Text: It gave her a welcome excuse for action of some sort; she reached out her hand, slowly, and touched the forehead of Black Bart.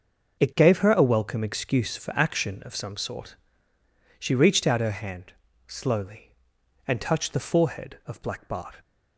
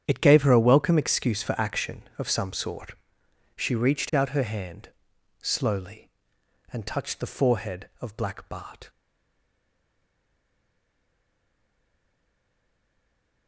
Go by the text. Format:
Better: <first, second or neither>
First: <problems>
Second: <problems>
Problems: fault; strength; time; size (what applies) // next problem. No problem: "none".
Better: first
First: starts louder than the rest; until 1.4 s; 6 dB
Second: starts louder than the rest; strong; until 1.0 s; 8.5 dB // stays silent after the last word; strong; from 8.8 s on; 4.6 s long